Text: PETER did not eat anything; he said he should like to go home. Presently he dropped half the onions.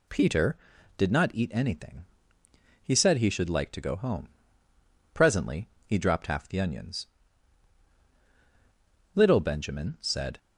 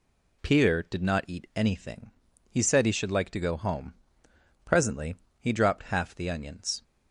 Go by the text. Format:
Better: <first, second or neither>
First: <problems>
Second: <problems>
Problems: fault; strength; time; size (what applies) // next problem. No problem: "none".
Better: second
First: pauses between "Presently" and "he"; slight; at 5.6 s; 0.16 s long // goes on to say "LITTLE Benjamin said"; noticeable; from 9.1 s on; 1.2 s long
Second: pauses between "Presently" and "he"; slight; at 5.1 s; 0.26 s long